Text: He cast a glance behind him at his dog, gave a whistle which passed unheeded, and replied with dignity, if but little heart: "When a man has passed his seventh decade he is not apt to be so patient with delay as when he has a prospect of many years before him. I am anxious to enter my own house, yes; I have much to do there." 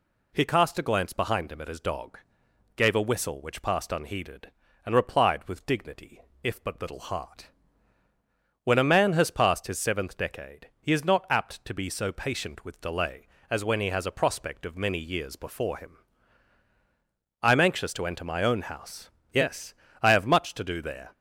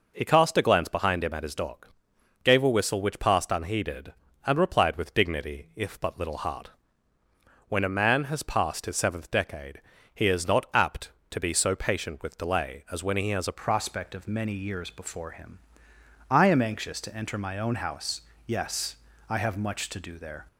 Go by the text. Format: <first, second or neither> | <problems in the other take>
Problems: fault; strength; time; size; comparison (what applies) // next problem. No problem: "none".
first | pauses between "decade" and "he"; slight; at 9.8 s; 0.34 s long // changes voice at "prospect"; from 13.5 s on; 6.9 s long